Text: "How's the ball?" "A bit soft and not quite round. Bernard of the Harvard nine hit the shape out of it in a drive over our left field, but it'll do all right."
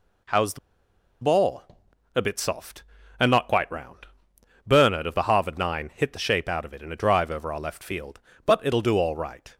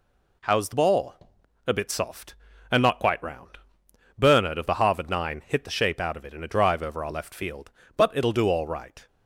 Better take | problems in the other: second | pauses between "the" and "ball"; noticeable; at 0.5 s; 0.64 s long

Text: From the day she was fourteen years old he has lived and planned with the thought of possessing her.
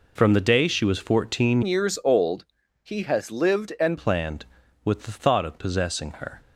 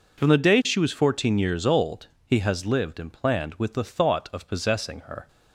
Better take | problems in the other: second | changes voice from "years" to "and"; from 1.6 to 3.9 s; 2.3 s long // pauses between "old" and "he"; at 2.4 s; 0.38 s long; slight in the second

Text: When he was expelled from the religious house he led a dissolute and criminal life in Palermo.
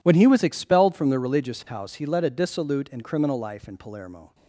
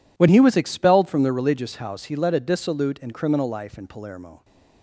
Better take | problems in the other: neither | none

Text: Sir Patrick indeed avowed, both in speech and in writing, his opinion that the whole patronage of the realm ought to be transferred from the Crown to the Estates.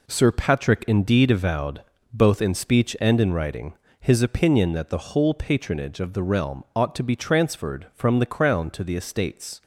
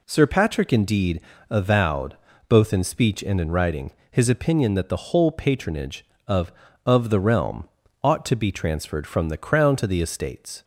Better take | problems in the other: first | pauses between "indeed" and "avowed"; slight; at 1.1 s; 0.30 s long // says "of" twice; at 6.8 s // pauses between "realm" and "ought"; at 7.6 s; 0.38 s long

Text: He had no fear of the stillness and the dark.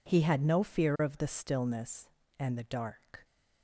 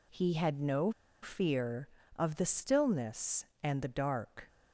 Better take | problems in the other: first | pauses between "no" and "fear"; slight; at 0.8 s; 0.32 s long

